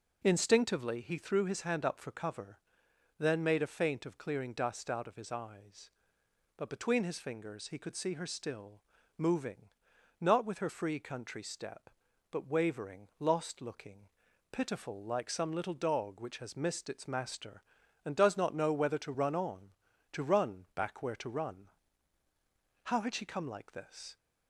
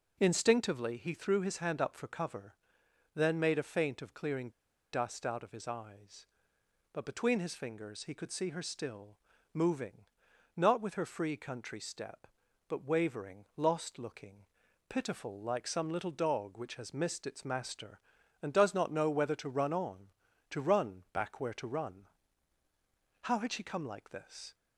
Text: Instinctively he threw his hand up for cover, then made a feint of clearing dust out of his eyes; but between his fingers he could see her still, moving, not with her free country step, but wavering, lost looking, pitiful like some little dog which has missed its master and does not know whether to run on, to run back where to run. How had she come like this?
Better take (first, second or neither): first